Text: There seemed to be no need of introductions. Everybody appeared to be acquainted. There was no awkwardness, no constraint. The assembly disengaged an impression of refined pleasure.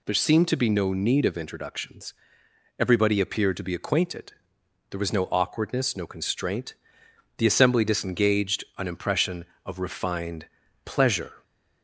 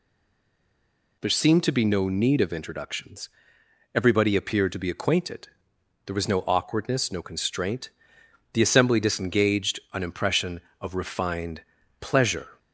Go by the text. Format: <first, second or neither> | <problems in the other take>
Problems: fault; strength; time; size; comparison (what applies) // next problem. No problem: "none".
first | stays silent before the first word; noticeable; until 1.2 s; 1.2 s long // pauses between "refined" and "pleasure"; at 11.6 s; 0.38 s long; also in the first